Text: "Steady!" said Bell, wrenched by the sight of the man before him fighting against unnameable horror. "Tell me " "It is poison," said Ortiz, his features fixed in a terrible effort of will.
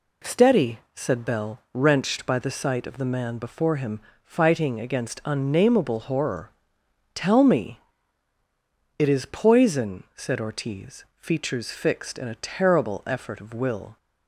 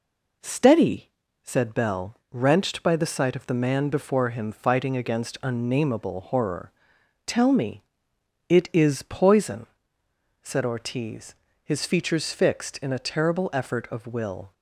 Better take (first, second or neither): second